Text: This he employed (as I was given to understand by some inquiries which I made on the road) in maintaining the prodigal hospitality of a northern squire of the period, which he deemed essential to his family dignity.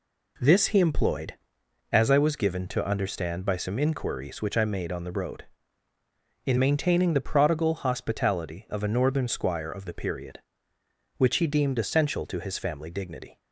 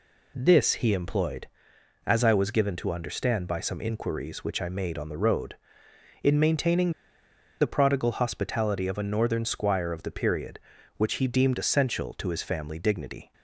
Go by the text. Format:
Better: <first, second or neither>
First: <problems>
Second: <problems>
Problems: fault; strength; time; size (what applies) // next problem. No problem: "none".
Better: first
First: none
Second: pauses between "maintaining" and "the"; noticeable; at 6.9 s; 0.69 s long